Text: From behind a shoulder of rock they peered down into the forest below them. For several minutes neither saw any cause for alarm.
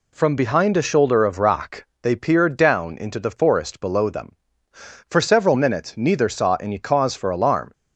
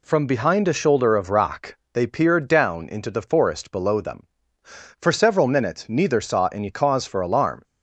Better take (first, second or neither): neither